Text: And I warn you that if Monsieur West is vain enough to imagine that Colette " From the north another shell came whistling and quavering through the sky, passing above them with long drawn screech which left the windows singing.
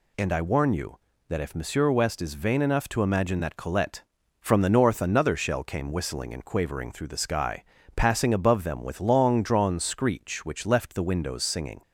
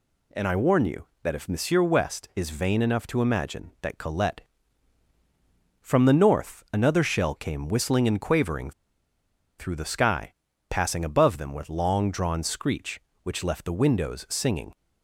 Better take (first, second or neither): first